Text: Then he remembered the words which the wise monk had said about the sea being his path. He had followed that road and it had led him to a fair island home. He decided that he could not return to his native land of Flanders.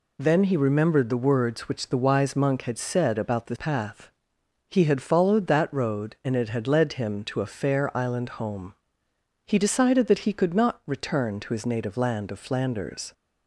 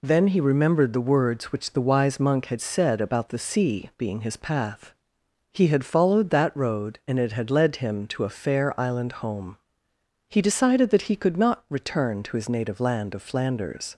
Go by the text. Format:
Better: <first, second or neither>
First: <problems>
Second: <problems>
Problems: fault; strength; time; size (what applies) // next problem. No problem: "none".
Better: second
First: skips "sea being his"; at 3.5 s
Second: none